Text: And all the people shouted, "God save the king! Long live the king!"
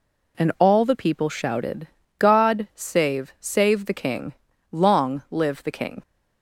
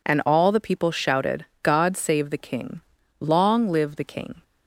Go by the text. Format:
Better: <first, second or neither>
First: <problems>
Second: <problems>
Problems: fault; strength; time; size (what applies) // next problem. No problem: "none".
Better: second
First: says "save" twice; at 3.3 s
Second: none